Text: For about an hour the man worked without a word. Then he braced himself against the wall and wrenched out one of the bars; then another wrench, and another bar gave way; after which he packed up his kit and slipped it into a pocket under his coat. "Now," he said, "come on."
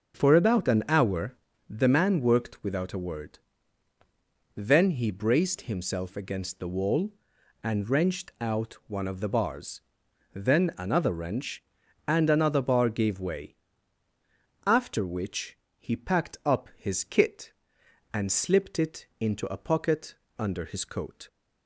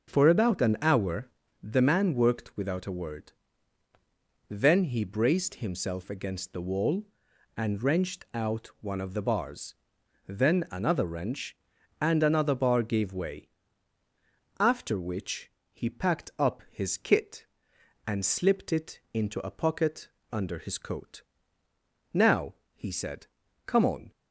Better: second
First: pauses between "hour" and "the"; slight; at 1.3 s; 0.34 s long // pauses between "which" and "he"; slight; at 15.5 s; 0.22 s long // pauses between "pocket" and "under"; slight; at 20.1 s; 0.24 s long // stops before "Now he said come on"; at 21.2 s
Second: pauses between "hour" and "the"; slight; at 1.2 s; 0.34 s long // pauses between "which" and "he"; slight; at 15.5 s; 0.22 s long // pauses between "pocket" and "under"; slight; at 20.0 s; 0.24 s long

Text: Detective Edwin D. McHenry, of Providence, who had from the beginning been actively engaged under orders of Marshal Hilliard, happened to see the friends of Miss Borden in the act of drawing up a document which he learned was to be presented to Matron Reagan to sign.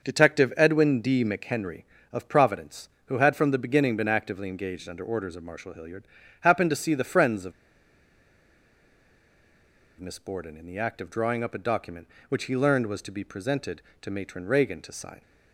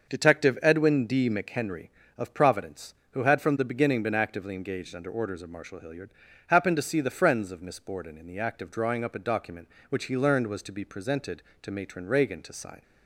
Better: second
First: starts louder than the rest; until 1.1 s; 6.5 dB // pauses between "of" and "Miss"; strong; at 7.5 s; 2.4 s long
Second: starts louder than the rest; until 1.1 s; 6.5 dB

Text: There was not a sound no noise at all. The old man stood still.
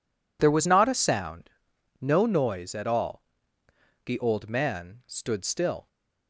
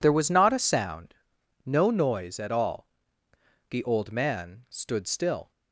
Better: neither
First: pauses between "sound" and "no"; noticeable; at 1.4 s; 0.50 s long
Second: pauses between "sound" and "no"; noticeable; at 1.1 s; 0.50 s long

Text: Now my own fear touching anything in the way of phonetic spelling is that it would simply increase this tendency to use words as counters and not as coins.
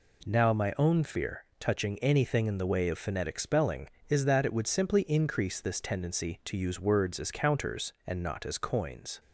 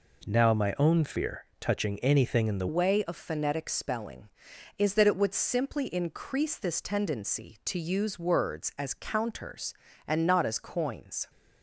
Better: first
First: none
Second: changes voice at "way"; from 2.6 s on; 8.6 s long

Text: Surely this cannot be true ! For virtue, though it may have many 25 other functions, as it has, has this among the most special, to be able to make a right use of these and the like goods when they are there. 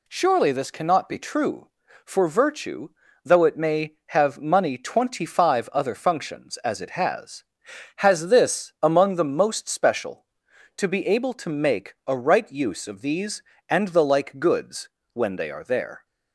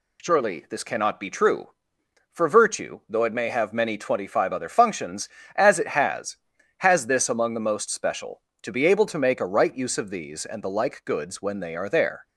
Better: second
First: says "money" for "many"; at 4.3 s // pauses between "goods" and "when"; slight; at 14.8 s; 0.26 s long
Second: none

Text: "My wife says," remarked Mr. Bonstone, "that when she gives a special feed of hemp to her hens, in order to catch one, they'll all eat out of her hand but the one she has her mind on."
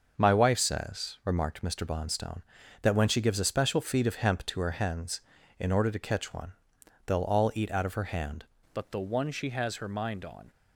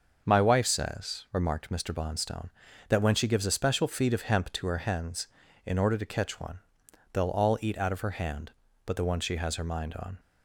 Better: second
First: starts louder than the rest; noticeable; until 1.1 s; 6 dB // changes voice at "but"; from 8.7 s on; 1.7 s long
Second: starts louder than the rest; until 1.2 s; 6 dB

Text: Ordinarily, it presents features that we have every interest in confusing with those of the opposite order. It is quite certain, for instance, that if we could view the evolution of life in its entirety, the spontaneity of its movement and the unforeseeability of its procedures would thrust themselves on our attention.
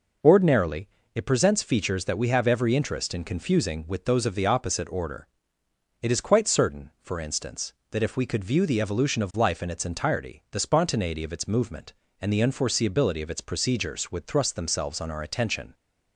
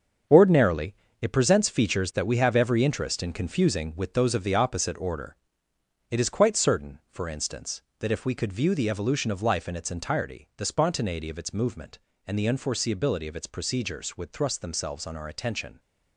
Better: first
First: none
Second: gets quieter; strong; throughout; 9.5 dB

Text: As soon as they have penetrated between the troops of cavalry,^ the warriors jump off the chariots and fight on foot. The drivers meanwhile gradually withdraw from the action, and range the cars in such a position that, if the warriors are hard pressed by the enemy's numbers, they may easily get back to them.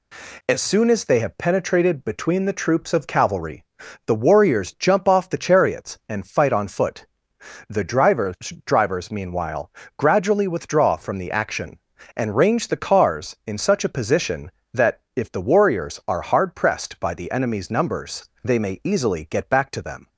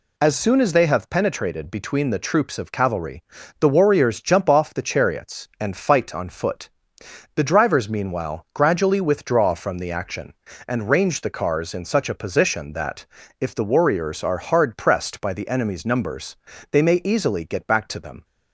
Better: second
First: says "drivers" twice; at 8.6 s // pauses between "meanwhile" and "gradually"; slight; at 9.7 s; 0.26 s long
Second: none

